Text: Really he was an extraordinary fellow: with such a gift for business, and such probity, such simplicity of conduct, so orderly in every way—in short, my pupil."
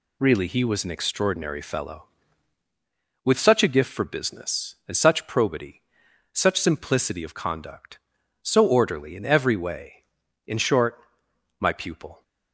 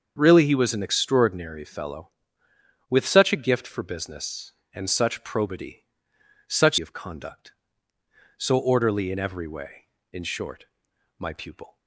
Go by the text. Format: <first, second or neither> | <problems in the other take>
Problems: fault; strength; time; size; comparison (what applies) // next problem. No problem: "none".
first | starts louder than the rest; until 1.1 s; 6.5 dB // skips "simplicity"; at 6.7 s